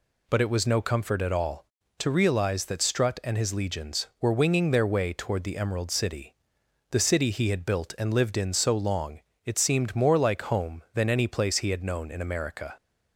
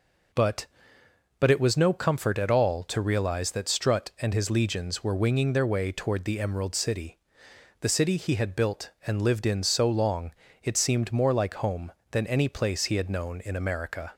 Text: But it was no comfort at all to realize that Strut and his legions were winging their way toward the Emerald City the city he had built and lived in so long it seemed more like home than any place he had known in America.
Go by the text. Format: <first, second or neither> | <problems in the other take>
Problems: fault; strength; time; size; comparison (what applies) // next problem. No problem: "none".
first | says "But" twice; at 1.3 s // pauses between "City" and "the"; noticeable; at 7.1 s; 0.62 s long; noticeable in the first // pauses between "long" and "it"; slight; at 10.3 s; 0.30 s long; slight in the first